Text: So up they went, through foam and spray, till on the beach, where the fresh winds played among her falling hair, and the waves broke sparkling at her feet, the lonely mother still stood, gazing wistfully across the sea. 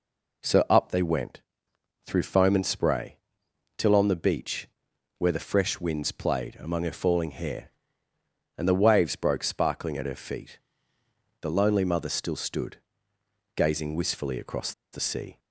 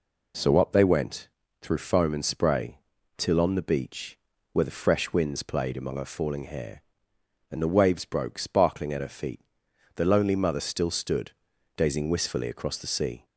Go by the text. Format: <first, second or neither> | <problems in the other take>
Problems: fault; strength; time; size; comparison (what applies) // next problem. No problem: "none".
second | pauses between "across" and "the"; slight; at 14.7 s; 0.20 s long